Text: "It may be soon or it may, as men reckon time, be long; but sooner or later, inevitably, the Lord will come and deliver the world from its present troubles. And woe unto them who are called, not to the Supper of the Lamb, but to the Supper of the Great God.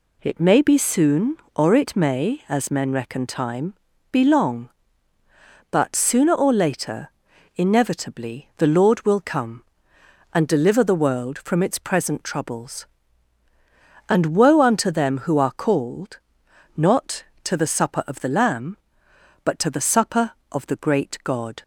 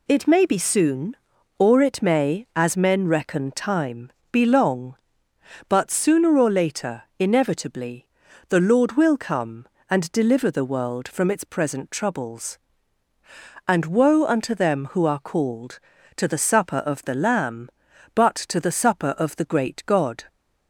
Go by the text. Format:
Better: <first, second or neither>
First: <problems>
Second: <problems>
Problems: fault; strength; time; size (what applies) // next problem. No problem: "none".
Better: first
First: none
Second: skips "not"; at 15.9 s